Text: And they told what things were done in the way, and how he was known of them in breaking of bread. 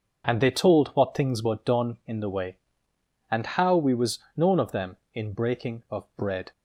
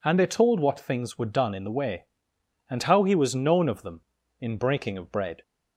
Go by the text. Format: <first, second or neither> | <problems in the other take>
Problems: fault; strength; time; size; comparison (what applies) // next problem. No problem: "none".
second | says "we" for "he"; at 3.7 s // pauses between "was" and "known"; slight; at 4.1 s; 0.18 s long